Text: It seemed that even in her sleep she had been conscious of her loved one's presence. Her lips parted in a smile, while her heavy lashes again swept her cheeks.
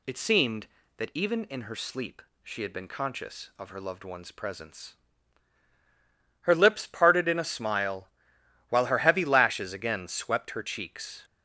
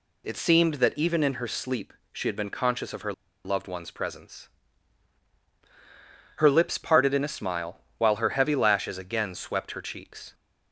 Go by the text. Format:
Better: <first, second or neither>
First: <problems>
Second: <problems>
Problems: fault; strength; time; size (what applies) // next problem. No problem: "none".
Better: first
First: pauses between "sleep" and "she"; slight; at 2.2 s; 0.20 s long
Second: pauses between "sleep" and "she"; slight; at 1.9 s; 0.18 s long // pauses between "her" and "loved"; slight; at 3.1 s; 0.31 s long